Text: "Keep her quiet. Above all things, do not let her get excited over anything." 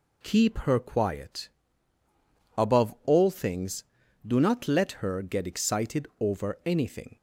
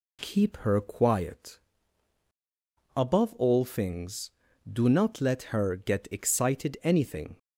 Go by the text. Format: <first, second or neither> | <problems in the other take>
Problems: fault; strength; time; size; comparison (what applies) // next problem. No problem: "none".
first | skips "over"; at 6.7 s